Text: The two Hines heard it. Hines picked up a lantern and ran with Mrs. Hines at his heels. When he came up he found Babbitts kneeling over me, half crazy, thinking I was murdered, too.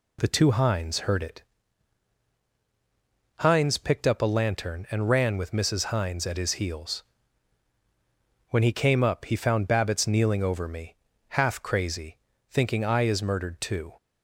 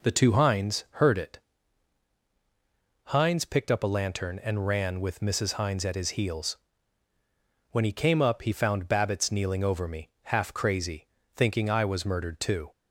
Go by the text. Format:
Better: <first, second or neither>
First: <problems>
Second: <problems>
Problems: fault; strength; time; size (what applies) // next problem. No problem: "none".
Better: second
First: says "is" for "was"; at 13.0 s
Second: none